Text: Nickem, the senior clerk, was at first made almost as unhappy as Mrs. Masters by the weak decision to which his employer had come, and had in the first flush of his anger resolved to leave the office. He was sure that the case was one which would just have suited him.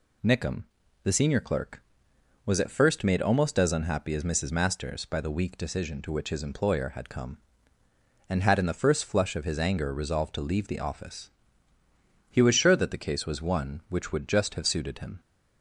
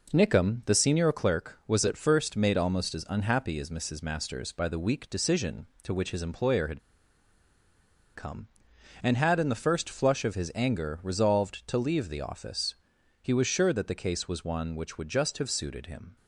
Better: first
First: none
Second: pauses between "had" and "come"; strong; at 6.7 s; 1.3 s long

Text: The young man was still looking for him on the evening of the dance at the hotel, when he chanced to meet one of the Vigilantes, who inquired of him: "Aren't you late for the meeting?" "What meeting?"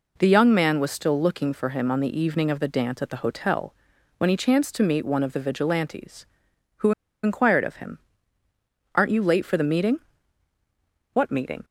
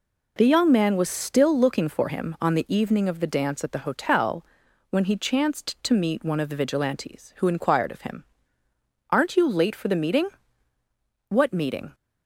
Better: second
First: pauses between "who" and "inquired"; slight; at 6.9 s; 0.32 s long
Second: none

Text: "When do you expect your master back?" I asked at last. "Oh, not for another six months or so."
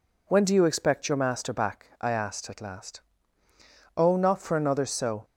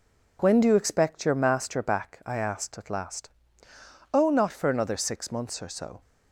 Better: second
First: skips "six months or"; at 4.8 s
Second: none

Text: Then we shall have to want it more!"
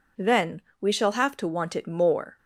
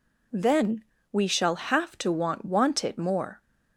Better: first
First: pauses between "Then" and "we"; slight; at 0.6 s; 0.18 s long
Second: pauses between "Then" and "we"; slight; at 0.8 s; 0.26 s long // says "want" twice; at 2.4 s

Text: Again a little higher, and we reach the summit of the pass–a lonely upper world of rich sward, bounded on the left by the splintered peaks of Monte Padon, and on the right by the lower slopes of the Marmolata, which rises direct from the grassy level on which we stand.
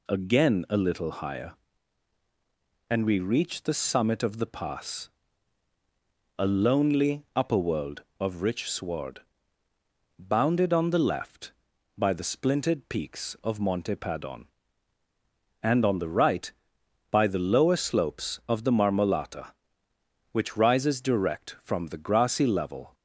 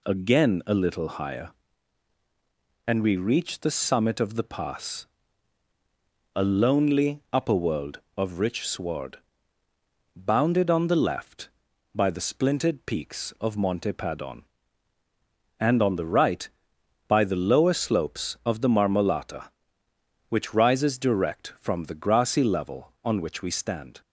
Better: second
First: stops before "on which we stand"; at 22.9 s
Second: none

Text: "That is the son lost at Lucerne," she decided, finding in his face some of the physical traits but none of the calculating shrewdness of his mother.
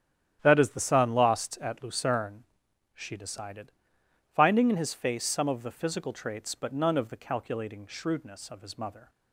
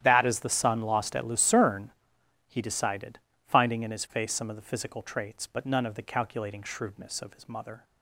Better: first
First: starts louder than the rest; strong; until 1.4 s; 10.5 dB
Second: starts louder than the rest; strong; until 1.0 s; 11 dB // says "he" for "she"; at 2.4 s

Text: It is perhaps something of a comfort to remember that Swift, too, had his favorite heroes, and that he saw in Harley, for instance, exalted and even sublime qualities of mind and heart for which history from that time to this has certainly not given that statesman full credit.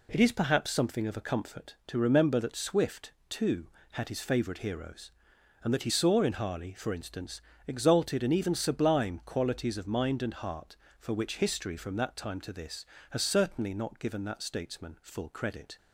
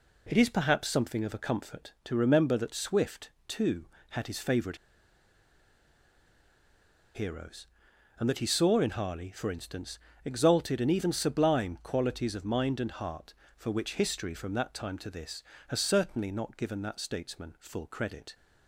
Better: first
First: none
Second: pauses between "favorite" and "heroes"; strong; at 4.7 s; 2.3 s long

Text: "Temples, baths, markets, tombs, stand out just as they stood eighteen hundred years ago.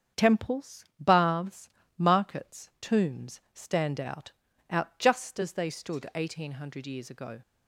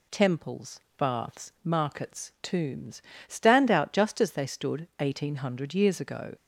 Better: second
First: starts louder than the rest; strong; until 1.3 s; 8 dB // says "out" twice; at 4.6 s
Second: none

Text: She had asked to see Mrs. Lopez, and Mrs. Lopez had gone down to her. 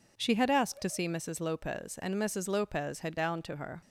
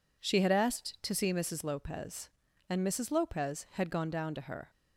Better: second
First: skips "gone"; at 3.1 s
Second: none

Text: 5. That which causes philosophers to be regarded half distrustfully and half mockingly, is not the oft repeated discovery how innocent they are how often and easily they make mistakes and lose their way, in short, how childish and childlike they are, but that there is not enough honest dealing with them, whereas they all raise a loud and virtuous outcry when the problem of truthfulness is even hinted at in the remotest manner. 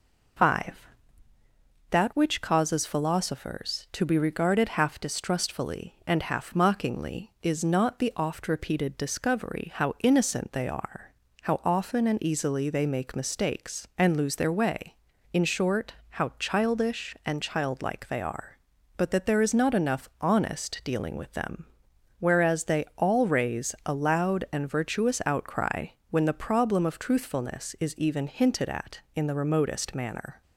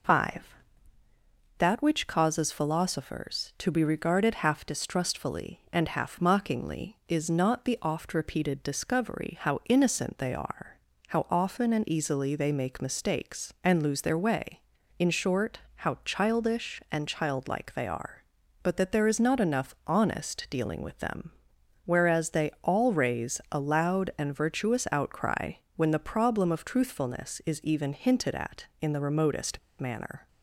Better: first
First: pauses between "are" and "how"; slight; at 11.1 s; 0.30 s long // pauses between "outcry" and "when"; slight; at 25.8 s; 0.22 s long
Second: pauses between "are" and "how"; slight; at 10.7 s; 0.30 s long // pauses between "outcry" and "when"; slight; at 25.5 s; 0.22 s long // pauses between "remotest" and "manner"; slight; at 29.5 s; 0.20 s long

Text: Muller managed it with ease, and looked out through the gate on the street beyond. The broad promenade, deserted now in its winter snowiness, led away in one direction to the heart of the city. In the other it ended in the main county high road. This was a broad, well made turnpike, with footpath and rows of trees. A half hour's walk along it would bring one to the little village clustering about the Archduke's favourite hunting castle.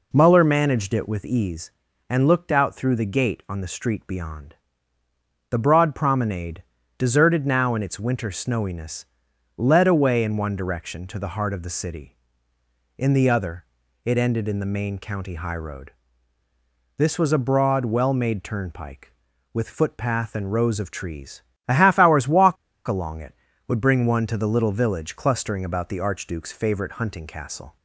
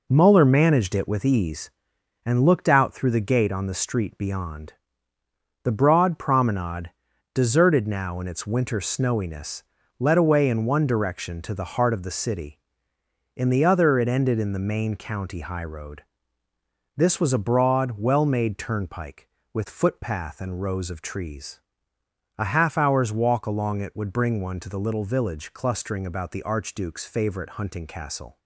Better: second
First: pauses between "other" and "it"; at 13.6 s; 0.38 s long // pauses between "walk" and "along"; slight; at 22.5 s; 0.31 s long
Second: none

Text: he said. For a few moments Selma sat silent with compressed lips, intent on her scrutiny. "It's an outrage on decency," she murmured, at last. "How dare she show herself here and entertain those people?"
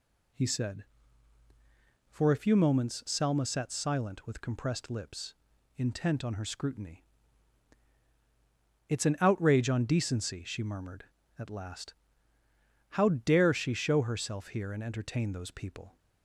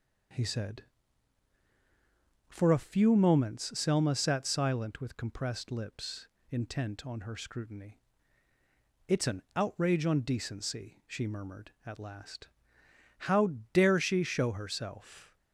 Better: first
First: none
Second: pauses between "How" and "dare"; slight; at 13.4 s; 0.26 s long // stops before "here and entertain those people"; at 15.3 s

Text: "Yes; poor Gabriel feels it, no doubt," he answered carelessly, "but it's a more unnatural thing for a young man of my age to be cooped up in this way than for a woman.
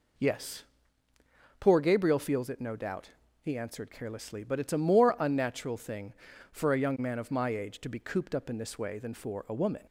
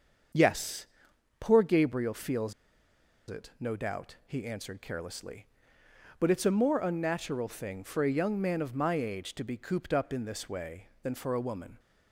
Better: first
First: none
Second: starts louder than the rest; until 1.8 s; 7 dB // pauses between "feels" and "it"; noticeable; at 2.5 s; 0.77 s long

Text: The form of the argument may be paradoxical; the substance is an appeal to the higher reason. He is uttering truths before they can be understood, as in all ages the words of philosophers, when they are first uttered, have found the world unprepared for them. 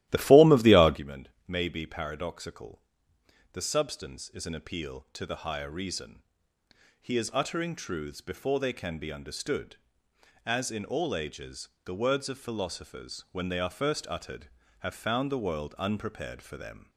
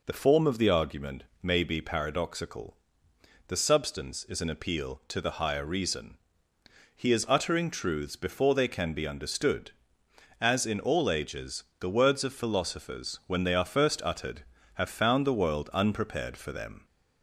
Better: second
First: starts louder than the rest; strong; until 1.0 s; 14.5 dB // pauses between "argument" and "may"; slight; at 1.2 s; 0.18 s long // pauses between "ages" and "the"; slight; at 11.6 s; 0.16 s long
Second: pauses between "argument" and "may"; slight; at 1.2 s; 0.18 s long // pauses between "ages" and "the"; slight; at 11.6 s; 0.16 s long

